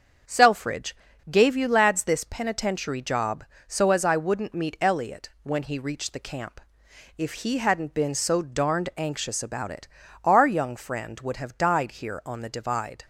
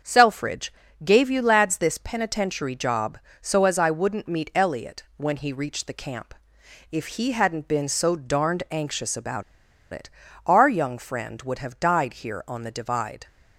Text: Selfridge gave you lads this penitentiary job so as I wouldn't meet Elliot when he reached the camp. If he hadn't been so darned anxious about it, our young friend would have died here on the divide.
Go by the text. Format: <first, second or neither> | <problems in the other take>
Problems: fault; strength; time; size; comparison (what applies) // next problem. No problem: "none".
first | starts louder than the rest; until 1.3 s; 7 dB; also in the first // pauses between "Selfridge" and "gave"; slight; at 0.7 s; 0.30 s long; slight in the first // pauses between "about" and "it"; noticeable; at 9.4 s; 0.49 s long